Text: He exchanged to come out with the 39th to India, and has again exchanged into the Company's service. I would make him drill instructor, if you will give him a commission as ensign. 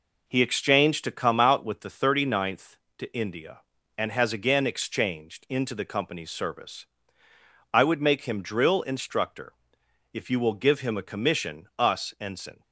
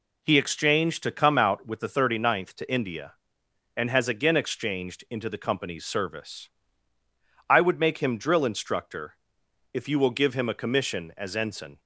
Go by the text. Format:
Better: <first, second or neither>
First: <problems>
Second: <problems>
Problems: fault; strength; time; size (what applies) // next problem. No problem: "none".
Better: second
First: says "us" for "as"; at 11.7 s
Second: none